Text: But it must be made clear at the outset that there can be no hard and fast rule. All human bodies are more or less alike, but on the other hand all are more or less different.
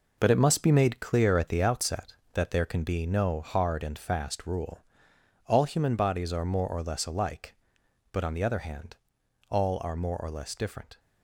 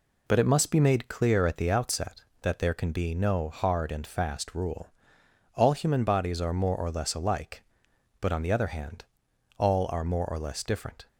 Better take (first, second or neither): second